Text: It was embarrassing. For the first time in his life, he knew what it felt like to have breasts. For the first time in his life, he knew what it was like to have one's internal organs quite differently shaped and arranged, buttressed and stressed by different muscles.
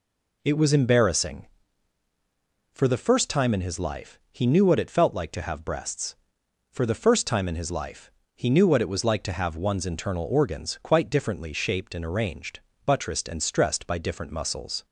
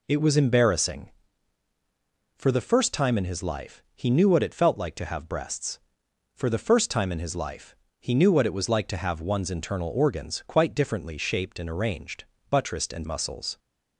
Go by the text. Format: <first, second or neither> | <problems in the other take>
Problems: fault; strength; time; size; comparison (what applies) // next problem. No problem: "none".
first | skips "stressed by different"; at 13.0 s